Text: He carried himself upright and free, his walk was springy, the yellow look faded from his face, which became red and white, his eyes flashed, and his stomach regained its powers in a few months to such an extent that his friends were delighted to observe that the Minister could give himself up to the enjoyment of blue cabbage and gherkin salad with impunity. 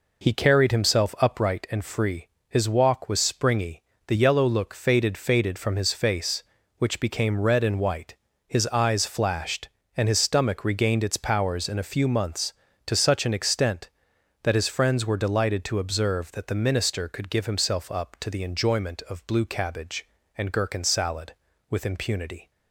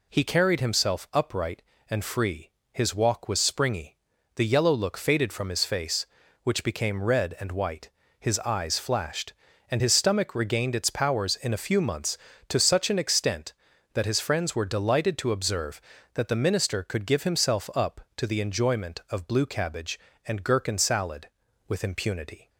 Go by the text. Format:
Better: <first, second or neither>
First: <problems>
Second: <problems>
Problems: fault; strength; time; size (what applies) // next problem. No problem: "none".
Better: second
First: says "faded" twice; at 5.1 s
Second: none